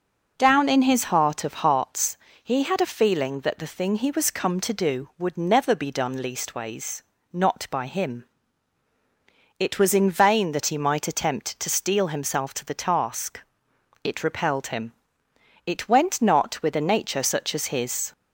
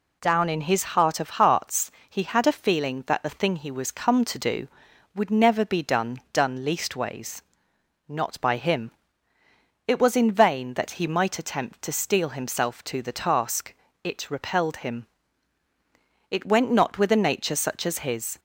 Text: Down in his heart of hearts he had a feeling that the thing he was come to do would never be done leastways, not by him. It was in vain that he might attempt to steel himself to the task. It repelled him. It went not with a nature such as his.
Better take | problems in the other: first | pauses between "hearts" and "he"; slight; at 1.9 s; 0.18 s long; slight in the first // says "done" twice; at 6.3 s

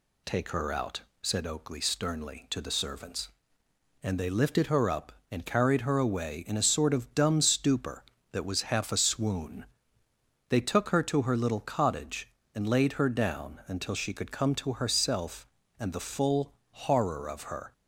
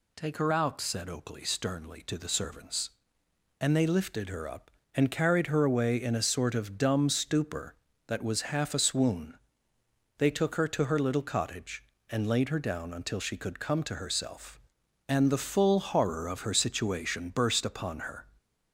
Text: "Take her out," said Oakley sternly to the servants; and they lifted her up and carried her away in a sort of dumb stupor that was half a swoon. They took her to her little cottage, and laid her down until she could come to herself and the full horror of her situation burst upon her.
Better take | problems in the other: second | pauses between "full" and "horror"; slight; at 16.5 s; 0.18 s long // stops before "situation burst upon her"; at 17.7 s

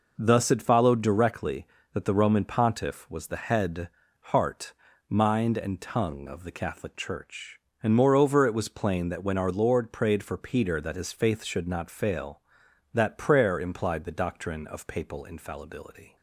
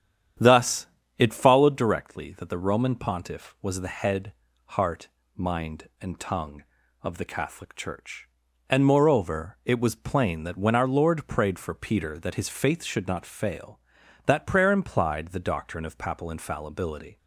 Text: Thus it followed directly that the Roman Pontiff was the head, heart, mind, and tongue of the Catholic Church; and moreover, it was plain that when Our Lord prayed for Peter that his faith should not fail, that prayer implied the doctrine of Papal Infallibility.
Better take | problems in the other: first | starts louder than the rest; strong; until 1.9 s; 9.5 dB // pauses between "Thus" and "it"; slight; at 0.8 s; 0.32 s long

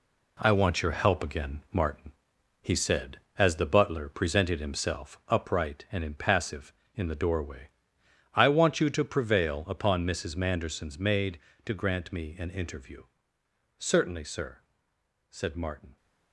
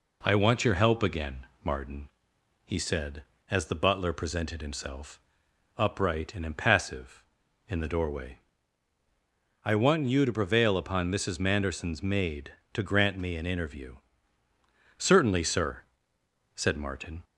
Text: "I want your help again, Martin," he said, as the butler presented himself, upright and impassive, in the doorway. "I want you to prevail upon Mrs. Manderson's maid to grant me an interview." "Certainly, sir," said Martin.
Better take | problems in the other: second | gets quieter; strong; throughout; 7 dB

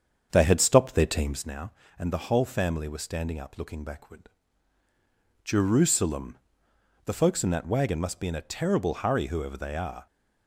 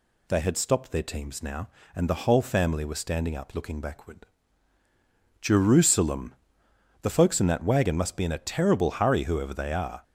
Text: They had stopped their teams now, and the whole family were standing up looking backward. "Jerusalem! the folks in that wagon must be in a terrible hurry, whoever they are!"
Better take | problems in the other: second | starts louder than the rest; strong; until 1.5 s; 7.5 dB

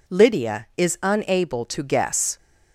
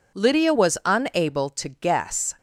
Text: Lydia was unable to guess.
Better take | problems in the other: second | says "is" for "was"; at 0.7 s

